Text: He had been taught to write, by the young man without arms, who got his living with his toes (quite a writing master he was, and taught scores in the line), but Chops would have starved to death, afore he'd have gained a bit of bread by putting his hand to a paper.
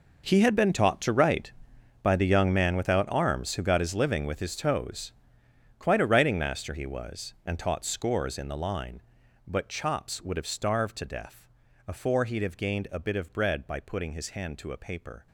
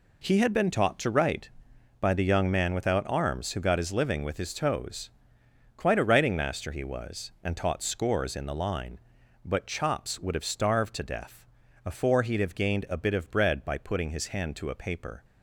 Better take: second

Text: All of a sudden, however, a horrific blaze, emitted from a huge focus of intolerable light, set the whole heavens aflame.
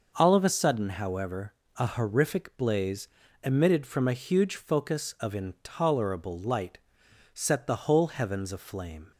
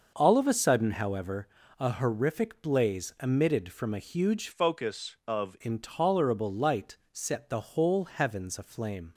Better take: first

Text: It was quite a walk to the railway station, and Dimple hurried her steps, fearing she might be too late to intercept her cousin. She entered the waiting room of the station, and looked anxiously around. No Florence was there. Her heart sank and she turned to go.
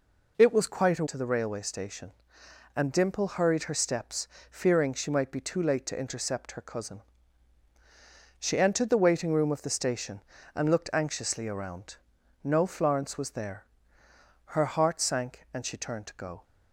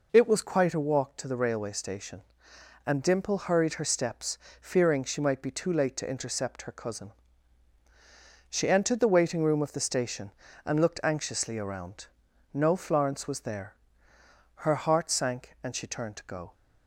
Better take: second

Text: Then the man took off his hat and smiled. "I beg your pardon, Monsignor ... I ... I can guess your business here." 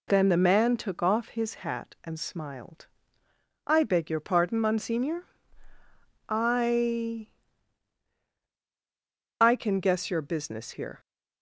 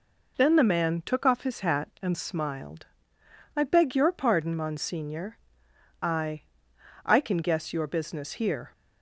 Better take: neither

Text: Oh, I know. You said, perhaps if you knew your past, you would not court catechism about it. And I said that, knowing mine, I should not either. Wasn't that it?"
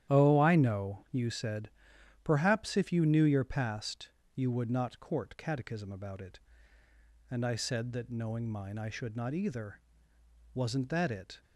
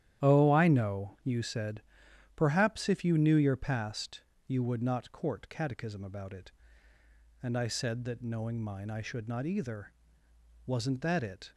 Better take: neither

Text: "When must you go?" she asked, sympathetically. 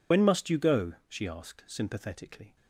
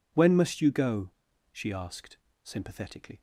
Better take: second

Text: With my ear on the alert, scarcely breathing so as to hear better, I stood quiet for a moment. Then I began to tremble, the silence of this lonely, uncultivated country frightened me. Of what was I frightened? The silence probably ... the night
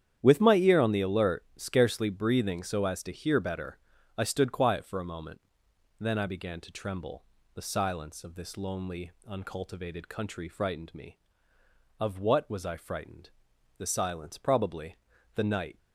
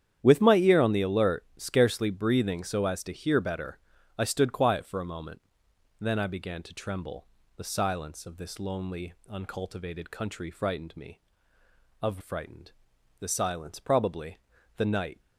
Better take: first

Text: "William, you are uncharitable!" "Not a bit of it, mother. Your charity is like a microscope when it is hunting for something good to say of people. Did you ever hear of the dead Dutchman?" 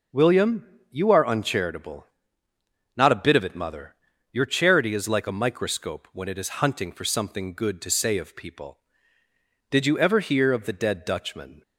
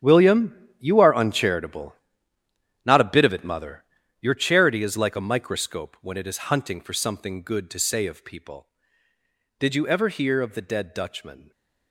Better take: first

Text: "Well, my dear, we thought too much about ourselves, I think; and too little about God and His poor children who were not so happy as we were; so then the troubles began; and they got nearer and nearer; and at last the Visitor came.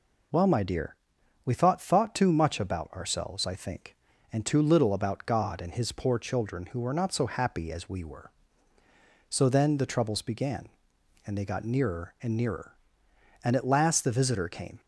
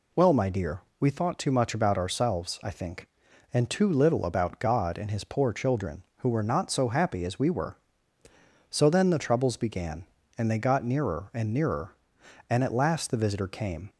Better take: second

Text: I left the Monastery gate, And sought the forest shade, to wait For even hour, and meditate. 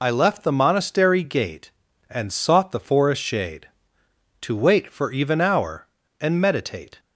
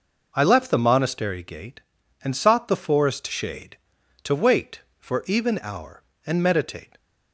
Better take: second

